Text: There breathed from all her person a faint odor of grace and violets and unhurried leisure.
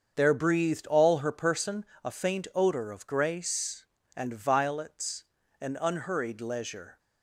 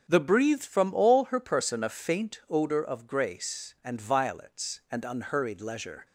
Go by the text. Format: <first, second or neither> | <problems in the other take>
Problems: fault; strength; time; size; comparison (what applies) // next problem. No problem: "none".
second | starts louder than the rest; until 1.1 s; 6.5 dB; also in the second // skips "from"; at 0.8 s // pauses between "person" and "a"; slight; at 1.8 s; 0.18 s long